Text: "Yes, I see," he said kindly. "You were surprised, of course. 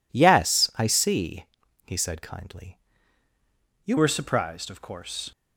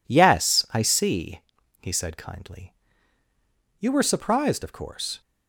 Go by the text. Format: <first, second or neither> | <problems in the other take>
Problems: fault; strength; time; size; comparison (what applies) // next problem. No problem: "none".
second | changes voice at "were"; from 3.9 s on; 1.4 s long